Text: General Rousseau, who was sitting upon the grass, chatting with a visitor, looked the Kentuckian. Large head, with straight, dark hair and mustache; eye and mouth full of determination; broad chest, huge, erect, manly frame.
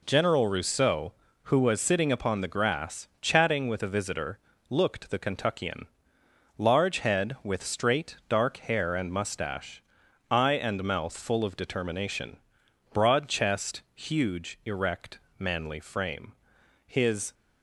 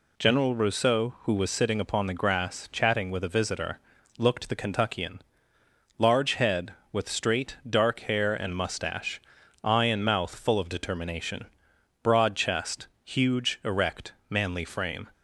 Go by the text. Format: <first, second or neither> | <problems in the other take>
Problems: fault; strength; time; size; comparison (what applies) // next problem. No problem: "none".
second | goes on to say "His"; slight; from 16.8 s on; 0.48 s long